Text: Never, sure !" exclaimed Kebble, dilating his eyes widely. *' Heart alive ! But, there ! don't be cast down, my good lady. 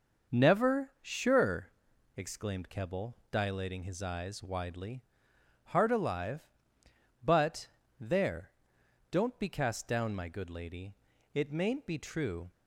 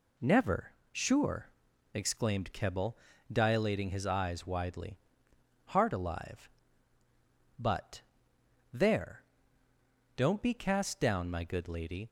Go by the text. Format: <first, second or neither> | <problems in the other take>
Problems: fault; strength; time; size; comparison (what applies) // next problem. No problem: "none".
second | starts louder than the rest; noticeable; until 1.4 s; 6 dB // goes on to say "It mayn't be true"; noticeable; from 11.3 s on; 1.1 s long